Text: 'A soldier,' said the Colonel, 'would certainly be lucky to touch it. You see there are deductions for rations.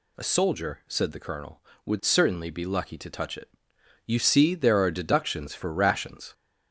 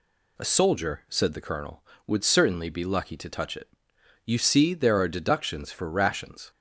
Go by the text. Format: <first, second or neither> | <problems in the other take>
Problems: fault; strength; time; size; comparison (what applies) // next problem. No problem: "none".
second | gets louder; slight; throughout; 3 dB